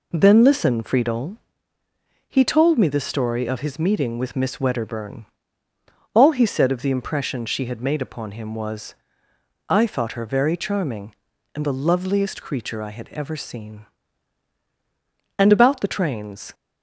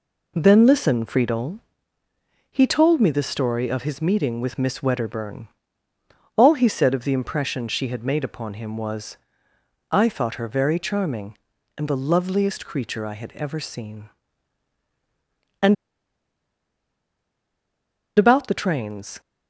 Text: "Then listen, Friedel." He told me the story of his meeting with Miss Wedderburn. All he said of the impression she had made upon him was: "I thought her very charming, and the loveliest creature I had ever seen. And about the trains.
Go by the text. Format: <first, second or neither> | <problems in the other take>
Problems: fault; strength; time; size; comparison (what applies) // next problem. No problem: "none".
first | pauses between "And" and "about"; strong; at 15.7 s; 2.4 s long